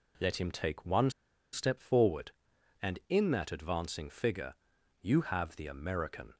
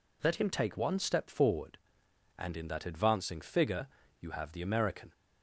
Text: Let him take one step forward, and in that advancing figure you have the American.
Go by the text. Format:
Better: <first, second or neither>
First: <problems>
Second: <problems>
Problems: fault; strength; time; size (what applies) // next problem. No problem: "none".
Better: second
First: pauses between "one" and "step"; at 1.0 s; 0.42 s long // pauses between "figure" and "you"; noticeable; at 4.5 s; 0.46 s long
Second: pauses between "figure" and "you"; slight; at 3.8 s; 0.33 s long